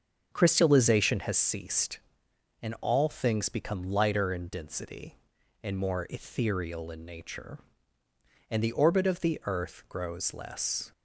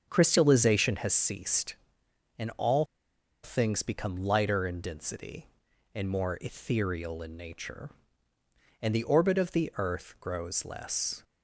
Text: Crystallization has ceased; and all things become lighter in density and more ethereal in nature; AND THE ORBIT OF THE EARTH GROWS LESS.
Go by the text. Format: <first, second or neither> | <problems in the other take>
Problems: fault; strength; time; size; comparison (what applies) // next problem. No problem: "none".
first | starts louder than the rest; until 1.1 s; 7 dB; also in the first // pauses between "all" and "things"; noticeable; at 2.8 s; 0.57 s long